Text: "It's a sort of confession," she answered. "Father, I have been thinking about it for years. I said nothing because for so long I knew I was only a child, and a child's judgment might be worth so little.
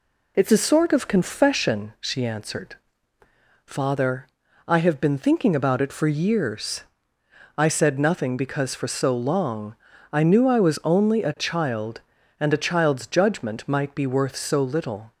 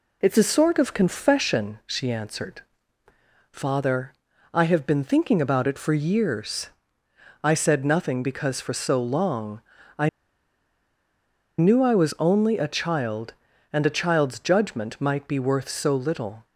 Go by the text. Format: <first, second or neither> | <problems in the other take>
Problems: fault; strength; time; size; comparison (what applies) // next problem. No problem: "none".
first | pauses between "long" and "I"; slight; at 9.6 s; 0.36 s long; slight in the first // pauses between "I" and "knew"; strong; at 10.0 s; 1.4 s long